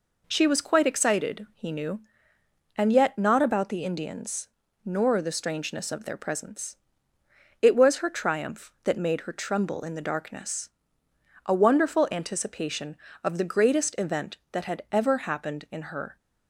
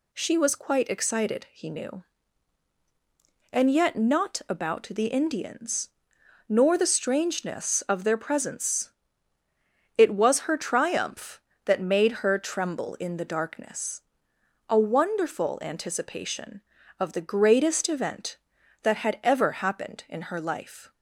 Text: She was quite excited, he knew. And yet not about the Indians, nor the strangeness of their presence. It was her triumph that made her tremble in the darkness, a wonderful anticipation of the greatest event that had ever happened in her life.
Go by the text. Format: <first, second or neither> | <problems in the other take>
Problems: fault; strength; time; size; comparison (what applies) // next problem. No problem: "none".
second | stops before "life"; at 16.1 s